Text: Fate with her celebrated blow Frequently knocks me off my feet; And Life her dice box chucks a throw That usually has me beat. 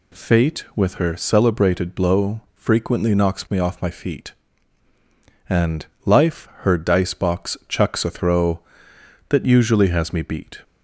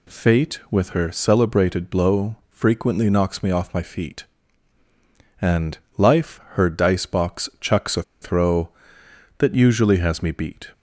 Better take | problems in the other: first | pauses between "And" and "Life"; slight; at 5.7 s; 0.22 s long; slight in the first // pauses between "a" and "throw"; slight; at 8.0 s; 0.19 s long

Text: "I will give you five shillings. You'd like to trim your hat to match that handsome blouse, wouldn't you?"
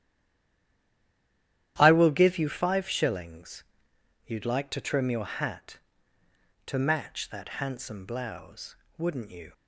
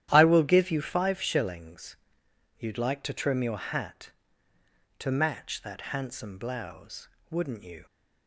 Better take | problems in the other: second | stays silent before the first word; noticeable; until 1.7 s; 1.7 s long // starts louder than the rest; strong; until 2.7 s; 11.5 dB; strong in the second

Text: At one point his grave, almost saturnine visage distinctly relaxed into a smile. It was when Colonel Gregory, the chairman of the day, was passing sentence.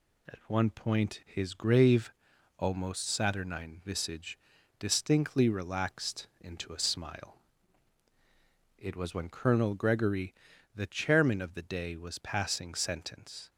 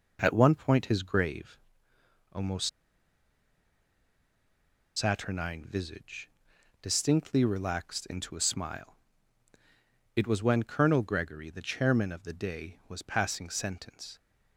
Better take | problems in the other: first | pauses between "almost" and "saturnine"; strong; at 2.6 s; 2.2 s long // pauses between "visage" and "distinctly"; noticeable; at 6.2 s; 0.52 s long; also in the first

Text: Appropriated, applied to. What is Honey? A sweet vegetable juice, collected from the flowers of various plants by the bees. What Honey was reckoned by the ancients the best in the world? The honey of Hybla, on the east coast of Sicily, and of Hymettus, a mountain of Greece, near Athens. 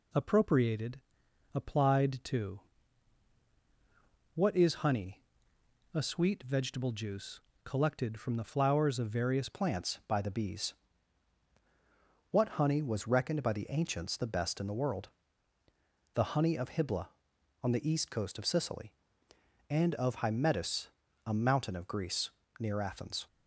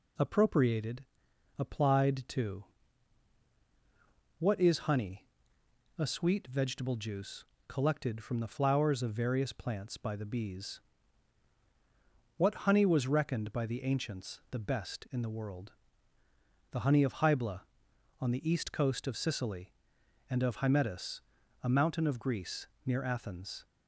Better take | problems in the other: second | changes voice at "plants"; from 9.4 s on; 13.8 s long

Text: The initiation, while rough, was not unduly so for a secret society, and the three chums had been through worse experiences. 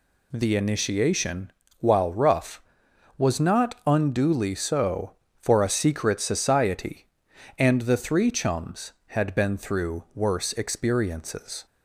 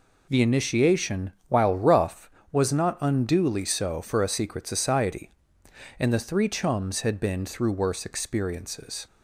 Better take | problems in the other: neither | none

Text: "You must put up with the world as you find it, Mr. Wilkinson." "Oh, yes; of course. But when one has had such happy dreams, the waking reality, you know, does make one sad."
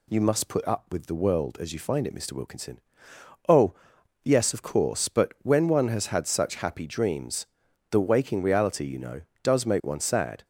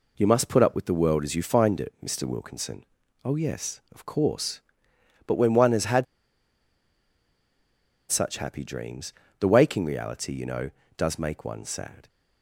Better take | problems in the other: first | pauses between "had" and "such"; strong; at 6.0 s; 2.0 s long

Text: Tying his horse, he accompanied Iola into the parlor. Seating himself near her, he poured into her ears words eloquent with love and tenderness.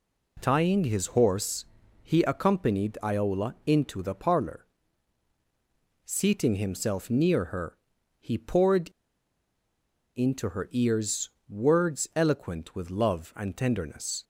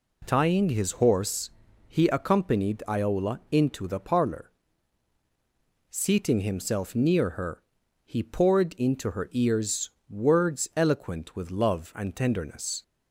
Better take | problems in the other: second | pauses between "poured" and "into"; strong; at 8.8 s; 1.2 s long // pauses between "ears" and "words"; slight; at 11.2 s; 0.18 s long; slight in the second

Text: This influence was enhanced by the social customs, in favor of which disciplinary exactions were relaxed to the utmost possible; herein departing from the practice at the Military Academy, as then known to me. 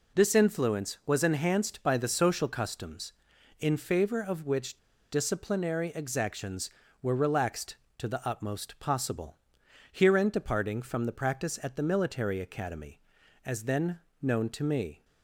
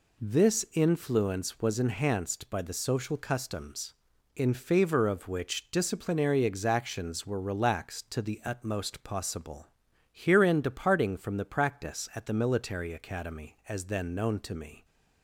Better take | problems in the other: second | pauses between "which" and "disciplinary"; slight; at 4.7 s; 0.33 s long // pauses between "then" and "known"; slight; at 14.0 s; 0.20 s long

